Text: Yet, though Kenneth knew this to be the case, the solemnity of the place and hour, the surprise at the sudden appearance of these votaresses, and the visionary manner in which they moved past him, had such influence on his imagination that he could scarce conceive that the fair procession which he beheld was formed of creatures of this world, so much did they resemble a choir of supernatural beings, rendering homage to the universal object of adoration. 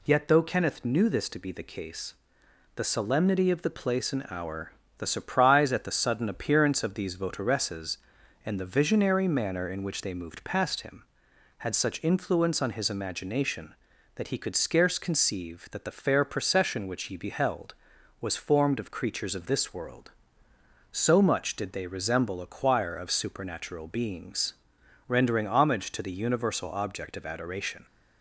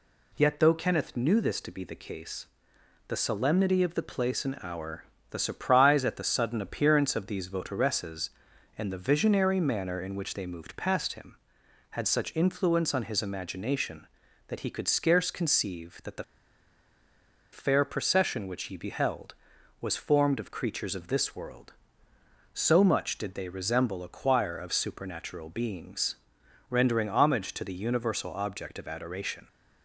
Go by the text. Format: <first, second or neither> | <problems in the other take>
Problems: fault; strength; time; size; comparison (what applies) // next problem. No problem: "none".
first | pauses between "the" and "fair"; strong; at 16.2 s; 1.2 s long